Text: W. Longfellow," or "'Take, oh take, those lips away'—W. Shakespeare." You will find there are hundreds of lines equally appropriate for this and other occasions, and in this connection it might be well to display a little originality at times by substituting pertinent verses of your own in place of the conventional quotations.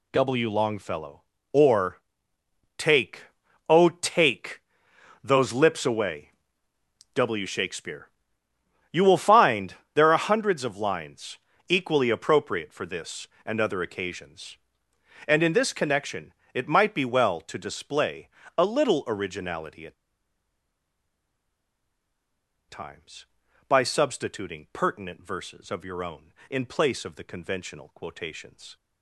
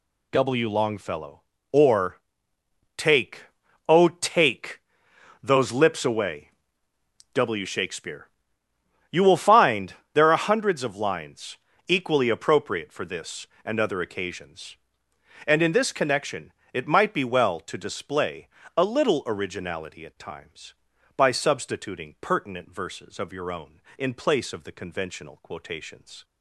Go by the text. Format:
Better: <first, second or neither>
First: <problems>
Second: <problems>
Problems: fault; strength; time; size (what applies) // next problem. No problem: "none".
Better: second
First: pauses between "or" and "Take"; noticeable; at 1.9 s; 0.78 s long // pauses between "find" and "there"; slight; at 9.7 s; 0.18 s long // pauses between "lines" and "equally"; slight; at 11.3 s; 0.30 s long // pauses between "connection" and "it"; slight; at 16.3 s; 0.22 s long // pauses between "display" and "a"; slight; at 18.2 s; 0.28 s long // pauses between "at" and "times"; strong; at 19.9 s; 2.7 s long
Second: pauses between "or" and "Take"; noticeable; at 2.1 s; 0.78 s long // pauses between "find" and "there"; slight; at 9.9 s; 0.18 s long // pauses between "lines" and "equally"; slight; at 11.5 s; 0.30 s long // pauses between "connection" and "it"; slight; at 16.5 s; 0.22 s long // pauses between "display" and "a"; slight; at 18.4 s; 0.28 s long